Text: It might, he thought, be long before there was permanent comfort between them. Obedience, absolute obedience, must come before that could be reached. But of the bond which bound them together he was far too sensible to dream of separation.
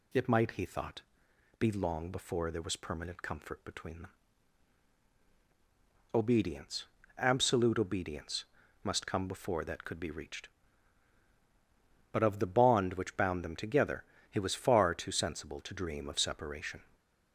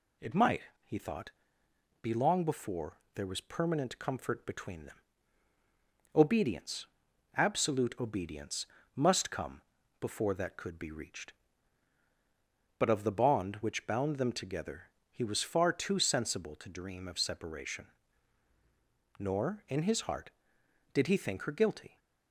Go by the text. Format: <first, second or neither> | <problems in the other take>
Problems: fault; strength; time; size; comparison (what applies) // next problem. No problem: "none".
first | pauses between "before" and "there"; slight; at 2.9 s; 0.16 s long // pauses between "come" and "before"; at 9.6 s; 0.40 s long // pauses between "together" and "he"; slight; at 14.9 s; 0.20 s long; slight in the first // goes on to say "Nor in his heart did he think her guilty"; strong; from 19.1 s on; 2.8 s long